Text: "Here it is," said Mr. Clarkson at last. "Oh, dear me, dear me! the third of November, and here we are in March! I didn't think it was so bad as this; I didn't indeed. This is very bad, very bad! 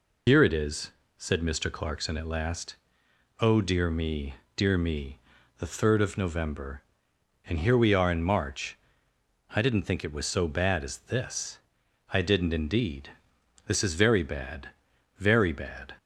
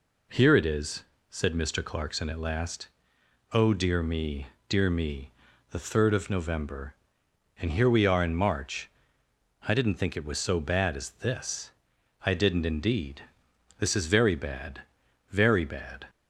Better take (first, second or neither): second